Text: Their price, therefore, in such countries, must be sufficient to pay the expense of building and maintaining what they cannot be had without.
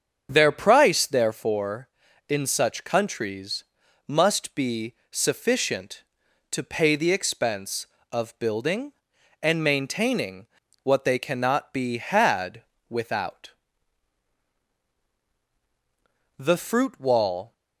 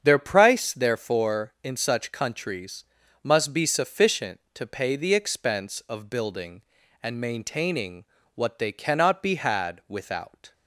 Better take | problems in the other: second | starts louder than the rest; strong; until 1.3 s; 7.5 dB; strong in the second // pauses between "be" and "sufficient"; slight; at 4.9 s; 0.16 s long // pauses between "maintaining" and "what"; at 10.4 s; 0.38 s long; slight in the second // pauses between "had" and "without"; slight; at 12.6 s; 0.26 s long // goes on to say "The fruit wall"; noticeable; from 16.3 s on; 1.1 s long

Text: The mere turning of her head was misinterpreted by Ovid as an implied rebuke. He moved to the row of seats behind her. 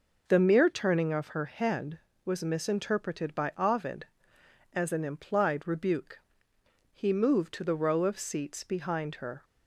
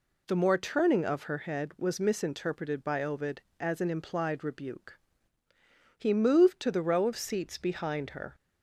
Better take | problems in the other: first | says "more" for "mere"; at 0.3 s

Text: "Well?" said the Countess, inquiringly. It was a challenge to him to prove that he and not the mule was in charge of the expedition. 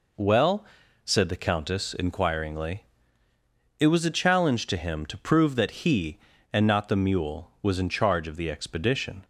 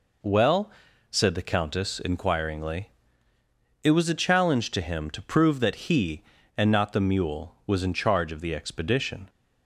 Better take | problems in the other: neither | none

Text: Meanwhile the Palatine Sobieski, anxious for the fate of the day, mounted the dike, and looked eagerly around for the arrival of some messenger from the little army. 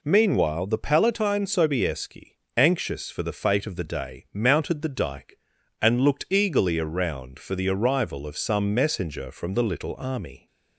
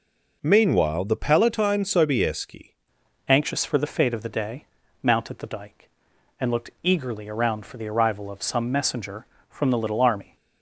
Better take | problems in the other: first | changes voice at "anxious"; from 3.2 s on; 7.1 s long

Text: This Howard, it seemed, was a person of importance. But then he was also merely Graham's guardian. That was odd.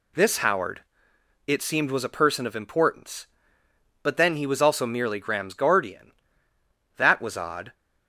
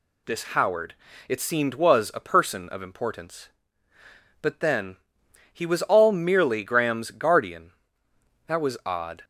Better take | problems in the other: first | pauses between "then" and "he"; noticeable; at 4.9 s; 0.56 s long // says "all" for "also"; at 5.8 s

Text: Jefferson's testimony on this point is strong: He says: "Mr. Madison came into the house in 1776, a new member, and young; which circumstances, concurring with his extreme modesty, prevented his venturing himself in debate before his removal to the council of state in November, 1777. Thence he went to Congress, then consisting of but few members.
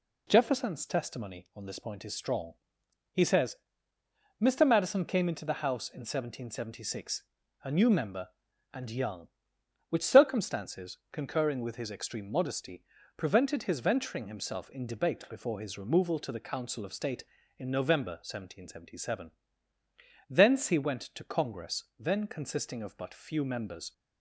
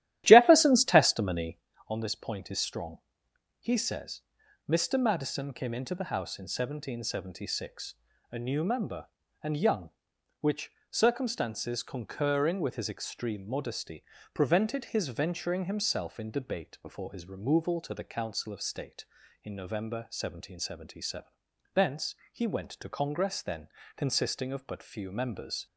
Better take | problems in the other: first | starts louder than the rest; strong; until 1.6 s; 13 dB // pauses between "which" and "circumstances"; slight; at 10.7 s; 0.18 s long // pauses between "Thence" and "he"; slight; at 22.1 s; 0.18 s long // pauses between "then" and "consisting"; slight; at 23.6 s; 0.30 s long

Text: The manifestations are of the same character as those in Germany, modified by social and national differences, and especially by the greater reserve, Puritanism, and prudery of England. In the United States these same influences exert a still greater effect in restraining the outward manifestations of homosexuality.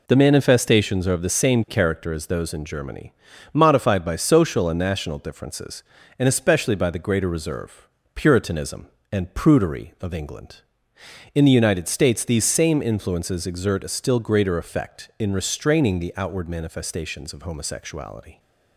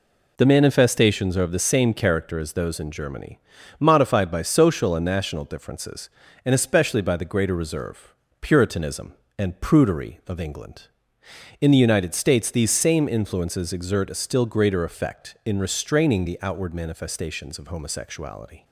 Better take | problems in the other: neither | none

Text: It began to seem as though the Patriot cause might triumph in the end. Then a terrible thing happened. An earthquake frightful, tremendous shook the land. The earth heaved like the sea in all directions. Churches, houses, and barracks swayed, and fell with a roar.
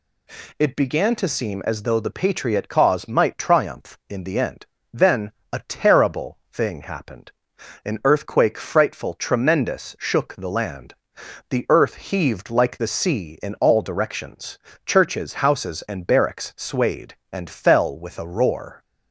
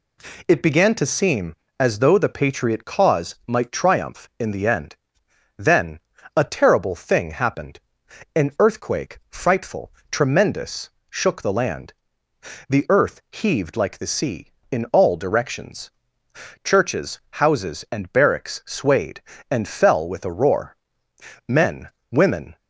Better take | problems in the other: first | pauses between "Then" and "a"; slight; at 6.0 s; 0.34 s long; slight in the first // pauses between "tremendous" and "shook"; slight; at 10.8 s; 0.20 s long // goes on to say "Men women"; noticeable; from 21.4 s on; 1.1 s long

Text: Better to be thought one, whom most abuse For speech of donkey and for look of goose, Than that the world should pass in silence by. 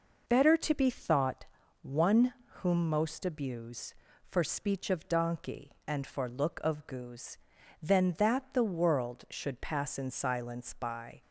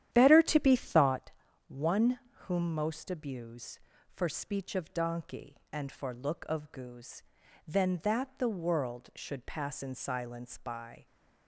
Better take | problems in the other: first | starts louder than the rest; strong; until 1.2 s; 11 dB // pauses between "thought" and "one"; at 1.3 s; 0.38 s long; also in the first

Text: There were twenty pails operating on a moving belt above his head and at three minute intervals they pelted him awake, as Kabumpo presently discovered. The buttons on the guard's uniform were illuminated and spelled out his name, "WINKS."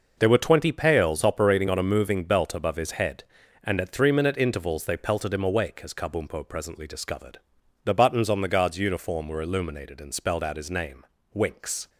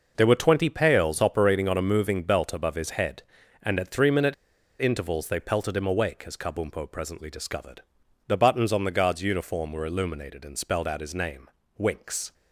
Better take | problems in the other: first | pauses between "minute" and "intervals"; noticeable; at 4.3 s; 0.46 s long

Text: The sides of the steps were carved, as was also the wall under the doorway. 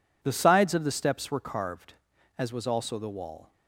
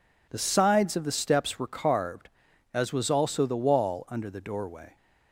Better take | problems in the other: second | stops before "under the doorway"; at 3.5 s

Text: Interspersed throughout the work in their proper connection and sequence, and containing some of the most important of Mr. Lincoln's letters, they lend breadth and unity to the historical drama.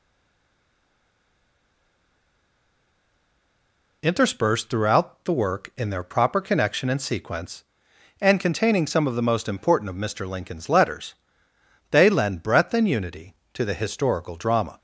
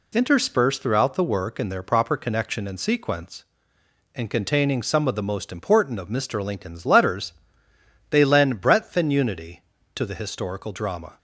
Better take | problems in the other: second | stays silent before the first word; strong; until 4.0 s; 4.0 s long

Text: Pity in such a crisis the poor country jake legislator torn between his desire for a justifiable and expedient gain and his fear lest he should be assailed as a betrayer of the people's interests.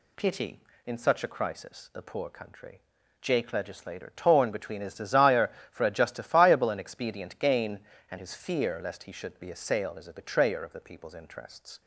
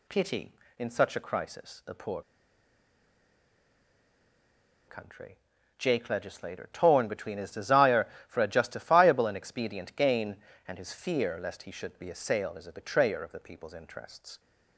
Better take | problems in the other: first | pauses between "poor" and "country"; strong; at 2.2 s; 2.6 s long // pauses between "country" and "jake"; at 5.3 s; 0.40 s long; also in the first

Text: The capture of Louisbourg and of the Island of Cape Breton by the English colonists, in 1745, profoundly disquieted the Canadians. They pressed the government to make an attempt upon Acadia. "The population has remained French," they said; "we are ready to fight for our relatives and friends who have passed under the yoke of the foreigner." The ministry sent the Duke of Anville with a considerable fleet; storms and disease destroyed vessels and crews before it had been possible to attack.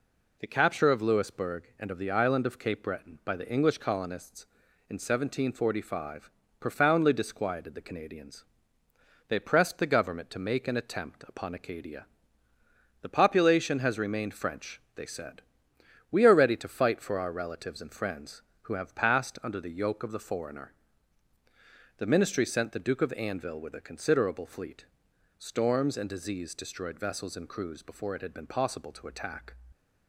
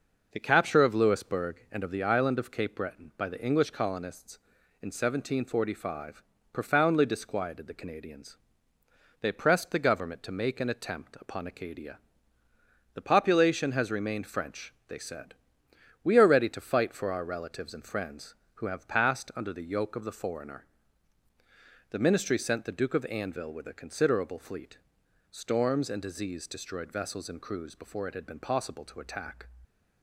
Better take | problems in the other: first | starts louder than the rest; noticeable; until 2.2 s; 5.5 dB

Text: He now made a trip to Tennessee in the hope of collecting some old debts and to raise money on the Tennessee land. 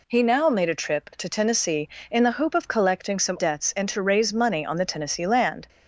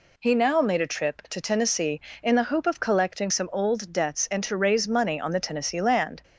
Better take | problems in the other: second | skips "old"; at 3.3 s

